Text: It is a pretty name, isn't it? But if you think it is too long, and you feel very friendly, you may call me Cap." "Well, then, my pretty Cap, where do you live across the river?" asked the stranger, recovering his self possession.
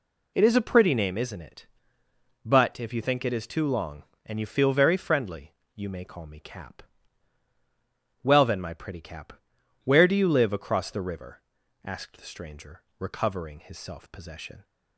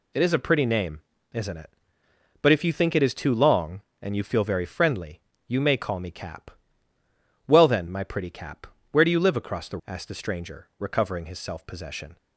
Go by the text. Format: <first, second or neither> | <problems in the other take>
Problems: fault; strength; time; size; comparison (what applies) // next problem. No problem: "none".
first | skips "river"; at 9.8 s